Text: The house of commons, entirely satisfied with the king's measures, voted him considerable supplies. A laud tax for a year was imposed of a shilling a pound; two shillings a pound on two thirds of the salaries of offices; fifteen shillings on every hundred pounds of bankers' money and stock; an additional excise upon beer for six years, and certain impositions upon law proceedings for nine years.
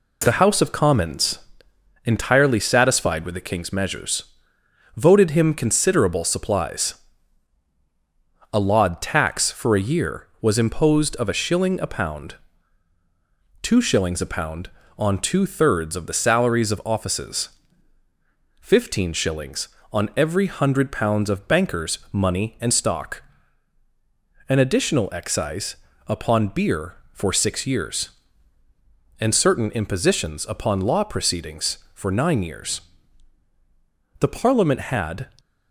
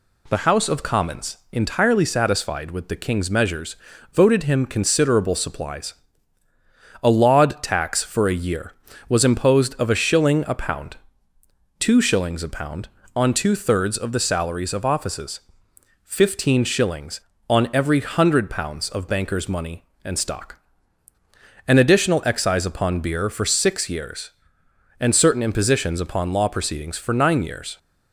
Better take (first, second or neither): second